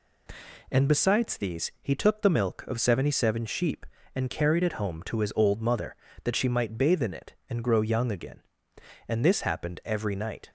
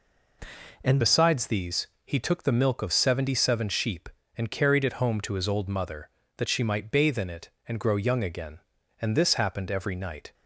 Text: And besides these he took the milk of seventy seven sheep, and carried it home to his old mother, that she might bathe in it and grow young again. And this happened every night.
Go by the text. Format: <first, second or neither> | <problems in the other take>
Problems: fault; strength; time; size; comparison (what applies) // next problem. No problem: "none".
first | changes voice at "besides"; from 1.0 s on; 9.3 s long // pauses between "these" and "he"; slight; at 1.8 s; 0.16 s long